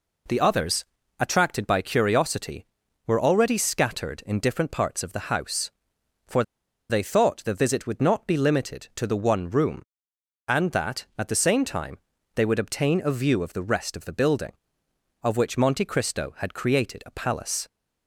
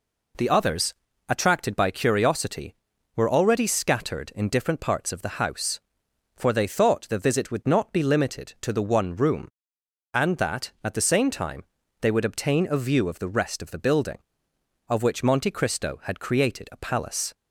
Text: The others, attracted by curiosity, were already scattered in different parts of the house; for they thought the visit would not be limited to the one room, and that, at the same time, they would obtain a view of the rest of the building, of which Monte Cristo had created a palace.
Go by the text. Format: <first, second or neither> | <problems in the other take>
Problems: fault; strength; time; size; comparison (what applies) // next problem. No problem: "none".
second | pauses between "for" and "they"; noticeable; at 6.4 s; 0.47 s long